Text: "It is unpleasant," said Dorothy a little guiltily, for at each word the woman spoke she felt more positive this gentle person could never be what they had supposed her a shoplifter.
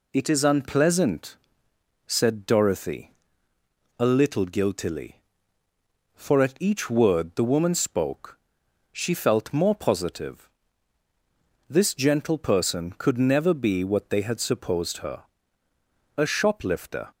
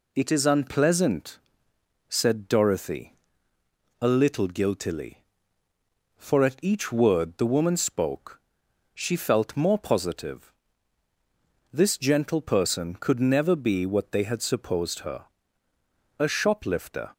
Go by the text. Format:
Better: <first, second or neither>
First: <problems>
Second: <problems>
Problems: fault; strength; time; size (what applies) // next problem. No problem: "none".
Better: neither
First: pauses between "Dorothy" and "a"; noticeable; at 3.1 s; 0.86 s long // pauses between "spoke" and "she"; noticeable; at 8.3 s; 0.52 s long // pauses between "positive" and "this"; at 10.4 s; 1.1 s long // pauses between "her" and "a"; noticeable; at 15.2 s; 0.92 s long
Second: pauses between "Dorothy" and "a"; noticeable; at 3.1 s; 0.86 s long // pauses between "spoke" and "she"; noticeable; at 8.4 s; 0.52 s long // pauses between "positive" and "this"; at 10.5 s; 1.1 s long // pauses between "her" and "a"; noticeable; at 15.2 s; 0.92 s long